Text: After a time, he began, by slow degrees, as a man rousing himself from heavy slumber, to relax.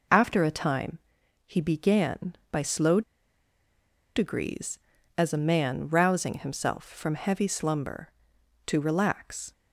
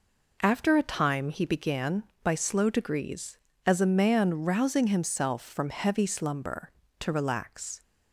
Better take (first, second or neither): second